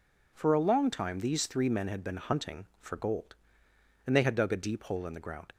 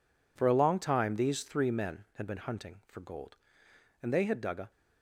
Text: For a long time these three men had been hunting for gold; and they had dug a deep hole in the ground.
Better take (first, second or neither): first